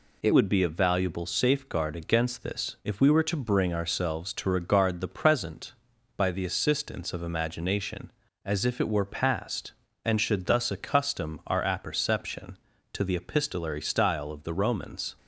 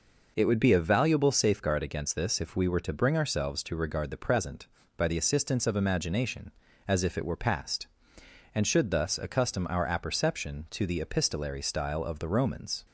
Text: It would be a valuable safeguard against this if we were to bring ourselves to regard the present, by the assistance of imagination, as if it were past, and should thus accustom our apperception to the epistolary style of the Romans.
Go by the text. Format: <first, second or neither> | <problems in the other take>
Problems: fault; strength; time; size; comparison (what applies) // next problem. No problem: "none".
second | changes voice at "would"; from 0.3 s on; 14.8 s long